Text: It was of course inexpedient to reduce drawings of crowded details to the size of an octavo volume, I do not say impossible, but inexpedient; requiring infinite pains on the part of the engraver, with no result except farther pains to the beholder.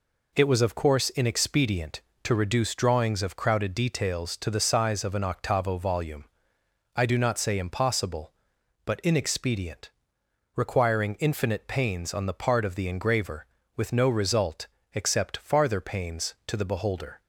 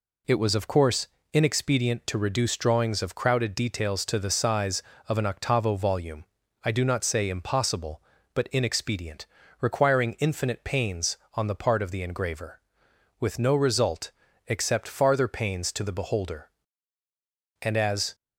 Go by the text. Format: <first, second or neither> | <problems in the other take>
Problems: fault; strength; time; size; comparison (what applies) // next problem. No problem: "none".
first | pauses between "course" and "inexpedient"; slight; at 1.0 s; 0.26 s long // pauses between "result" and "except"; slight; at 14.1 s; 0.34 s long; slight in the first // goes on to say "And as"; from 17.6 s on; 0.54 s long